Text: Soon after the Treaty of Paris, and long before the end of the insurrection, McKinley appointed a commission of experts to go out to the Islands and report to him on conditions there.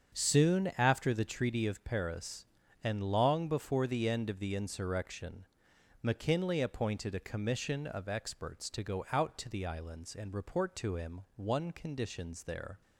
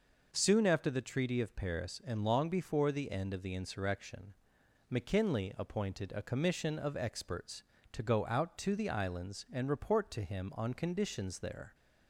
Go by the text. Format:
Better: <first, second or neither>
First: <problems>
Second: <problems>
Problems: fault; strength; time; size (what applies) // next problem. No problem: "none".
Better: second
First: starts louder than the rest; until 1.2 s; 7 dB // says "one" for "on"; at 11.3 s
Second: none